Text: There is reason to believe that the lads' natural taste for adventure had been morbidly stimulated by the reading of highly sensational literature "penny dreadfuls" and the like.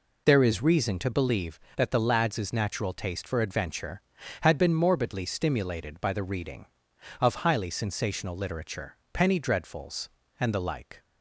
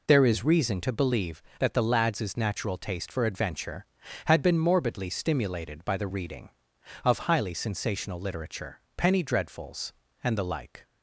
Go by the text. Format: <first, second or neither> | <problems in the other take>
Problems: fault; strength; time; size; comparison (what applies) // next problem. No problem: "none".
neither | pauses between "literature" and "penny"; slight; the same in both